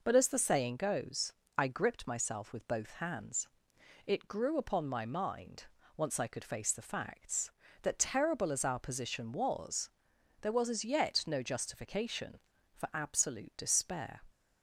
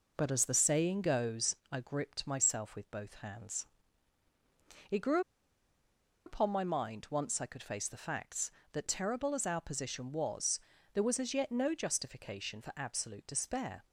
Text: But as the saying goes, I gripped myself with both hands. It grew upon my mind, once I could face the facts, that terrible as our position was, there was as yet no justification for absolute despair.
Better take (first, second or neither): first